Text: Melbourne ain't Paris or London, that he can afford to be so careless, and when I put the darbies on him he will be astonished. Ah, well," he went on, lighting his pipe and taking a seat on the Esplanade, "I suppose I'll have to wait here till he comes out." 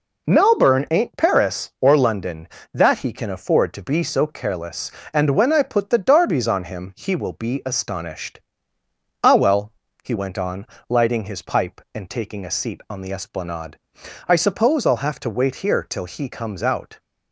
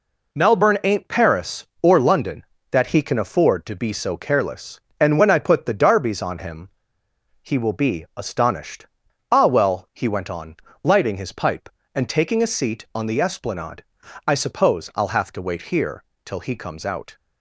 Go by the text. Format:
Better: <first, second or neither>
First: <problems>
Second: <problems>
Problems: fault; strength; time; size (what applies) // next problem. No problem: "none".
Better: first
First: none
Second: pauses between "him" and "he"; noticeable; at 6.6 s; 0.71 s long // pauses between "here" and "till"; slight; at 16.0 s; 0.22 s long